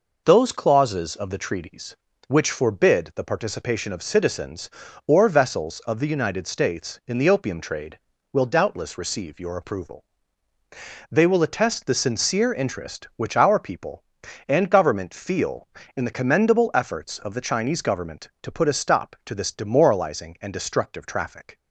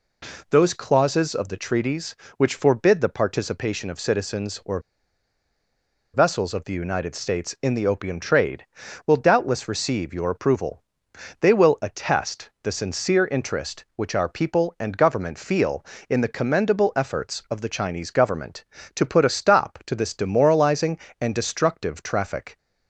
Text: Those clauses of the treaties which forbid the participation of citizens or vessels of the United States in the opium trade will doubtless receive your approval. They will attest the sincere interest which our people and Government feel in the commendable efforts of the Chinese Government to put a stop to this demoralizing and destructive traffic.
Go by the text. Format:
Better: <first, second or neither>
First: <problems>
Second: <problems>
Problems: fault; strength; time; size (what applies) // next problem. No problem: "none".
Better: first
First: none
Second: pauses between "or" and "vessels"; strong; at 4.7 s; 1.3 s long